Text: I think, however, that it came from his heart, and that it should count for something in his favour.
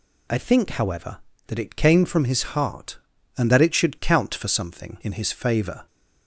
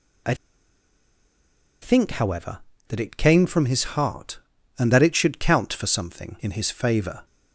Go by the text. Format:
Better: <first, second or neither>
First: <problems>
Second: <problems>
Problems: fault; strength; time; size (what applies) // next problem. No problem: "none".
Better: first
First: none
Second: pauses between "I" and "think"; strong; at 0.3 s; 1.4 s long